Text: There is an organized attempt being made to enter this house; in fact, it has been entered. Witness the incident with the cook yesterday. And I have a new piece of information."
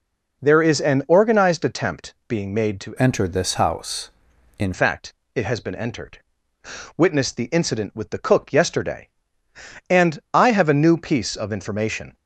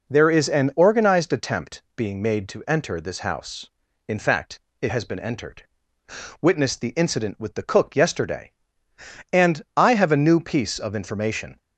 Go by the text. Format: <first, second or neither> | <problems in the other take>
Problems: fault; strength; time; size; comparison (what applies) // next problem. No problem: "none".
second | pauses between "attempt" and "being"; slight; at 2.1 s; 0.16 s long; slight in the second // changes voice from "enter" to "in"; from 2.9 to 4.7 s; 1.8 s long // pauses between "And" and "I"; slight; at 10.1 s; 0.16 s long; slight in the second